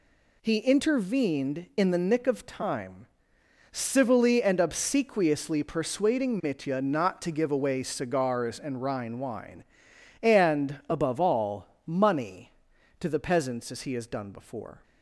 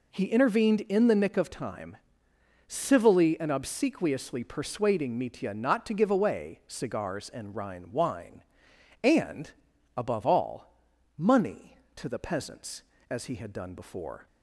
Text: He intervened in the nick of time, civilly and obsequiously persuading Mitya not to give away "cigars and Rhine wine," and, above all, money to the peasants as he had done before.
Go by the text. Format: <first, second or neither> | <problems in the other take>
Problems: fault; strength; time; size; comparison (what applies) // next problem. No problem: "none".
second | says "has" for "had"; at 13.9 s